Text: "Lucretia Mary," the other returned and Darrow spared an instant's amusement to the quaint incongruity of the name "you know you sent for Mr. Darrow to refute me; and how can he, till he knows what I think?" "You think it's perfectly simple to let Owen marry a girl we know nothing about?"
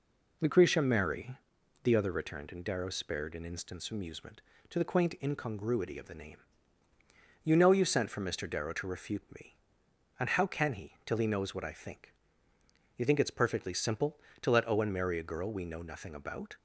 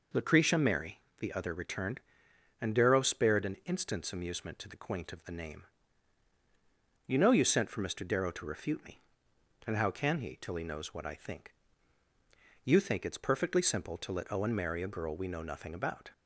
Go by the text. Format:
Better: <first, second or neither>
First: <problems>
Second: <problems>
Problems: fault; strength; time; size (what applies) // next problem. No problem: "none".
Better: first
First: pauses between "name" and "you"; at 6.4 s; 1.0 s long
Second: skips "incongruity"; at 5.1 s // pauses between "name" and "you"; strong; at 5.6 s; 1.4 s long